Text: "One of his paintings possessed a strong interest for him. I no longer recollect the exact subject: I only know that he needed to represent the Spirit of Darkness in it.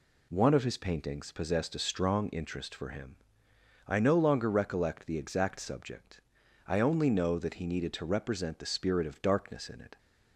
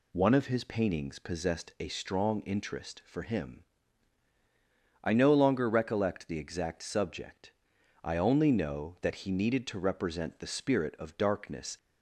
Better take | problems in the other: first | stops before "in it"; at 11.7 s

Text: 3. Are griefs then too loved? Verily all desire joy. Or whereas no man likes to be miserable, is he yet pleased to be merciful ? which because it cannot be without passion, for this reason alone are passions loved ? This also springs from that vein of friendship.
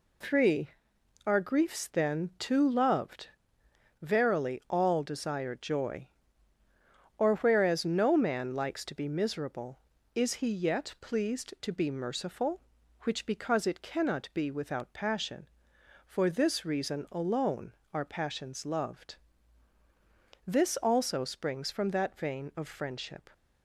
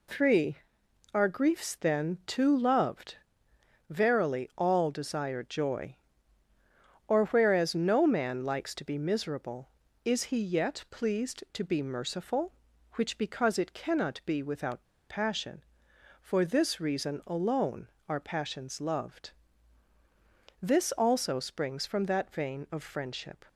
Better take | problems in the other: first | pauses between "without" and "passion"; slight; at 14.8 s; 0.25 s long

